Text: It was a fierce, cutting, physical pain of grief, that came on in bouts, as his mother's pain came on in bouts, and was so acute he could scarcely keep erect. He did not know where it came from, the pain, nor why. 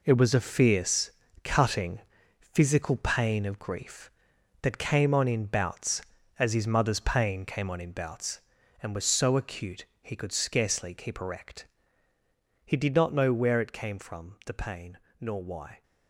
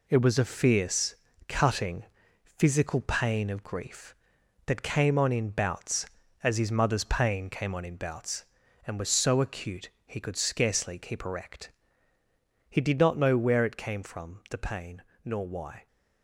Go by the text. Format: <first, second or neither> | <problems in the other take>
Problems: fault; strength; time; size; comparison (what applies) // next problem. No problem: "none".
second | gets quieter; strong; throughout; 9.5 dB // pauses between "acute" and "he"; slight; at 9.8 s; 0.18 s long; slight in the second